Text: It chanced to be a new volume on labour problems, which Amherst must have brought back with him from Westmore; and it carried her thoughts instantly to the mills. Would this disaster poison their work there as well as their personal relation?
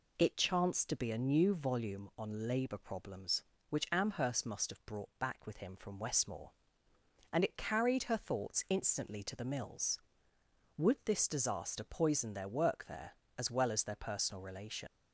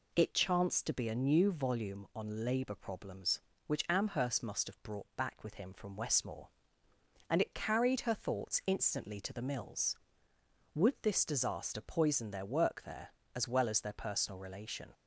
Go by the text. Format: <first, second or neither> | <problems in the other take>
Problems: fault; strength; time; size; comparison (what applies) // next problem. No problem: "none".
second | leaves "relation" unfinished; at 14.8 s; 90 ms